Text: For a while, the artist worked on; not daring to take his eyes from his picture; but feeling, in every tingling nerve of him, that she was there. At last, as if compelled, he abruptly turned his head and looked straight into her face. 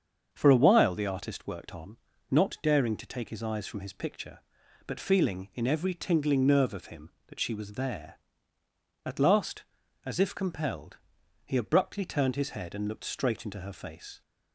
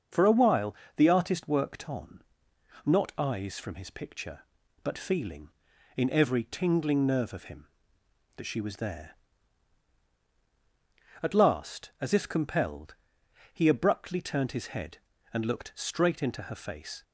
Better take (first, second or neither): first